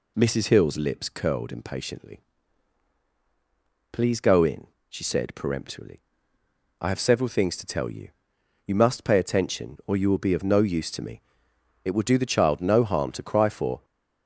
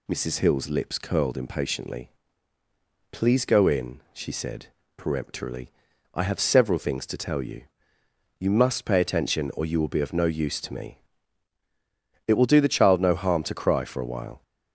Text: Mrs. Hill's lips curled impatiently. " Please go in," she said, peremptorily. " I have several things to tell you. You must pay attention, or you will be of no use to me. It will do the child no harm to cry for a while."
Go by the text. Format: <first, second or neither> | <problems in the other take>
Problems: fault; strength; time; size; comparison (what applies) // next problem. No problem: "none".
second | stops before "a while"; at 13.8 s